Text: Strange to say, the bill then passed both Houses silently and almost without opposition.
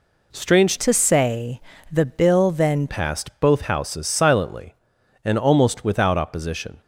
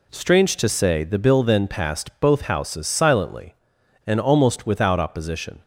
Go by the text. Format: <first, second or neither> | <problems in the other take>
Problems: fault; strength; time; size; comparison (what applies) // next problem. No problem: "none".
second | changes voice from "to" to "then"; from 0.7 to 2.8 s; 2.1 s long